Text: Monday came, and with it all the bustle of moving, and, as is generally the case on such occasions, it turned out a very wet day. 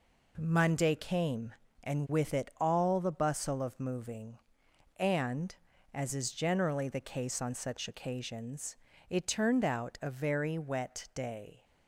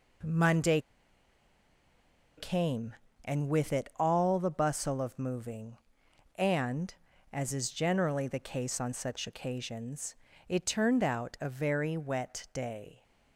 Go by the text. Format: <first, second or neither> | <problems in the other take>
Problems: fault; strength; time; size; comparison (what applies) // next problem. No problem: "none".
first | pauses between "Monday" and "came"; strong; at 0.7 s; 1.5 s long